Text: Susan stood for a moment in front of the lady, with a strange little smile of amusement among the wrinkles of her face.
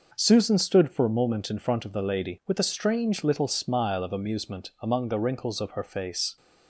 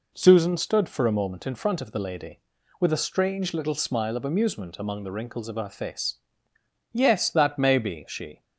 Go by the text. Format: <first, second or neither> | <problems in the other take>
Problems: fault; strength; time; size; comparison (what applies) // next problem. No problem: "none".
first | goes on to say "Yes that may be she"; from 6.9 s on; 1.5 s long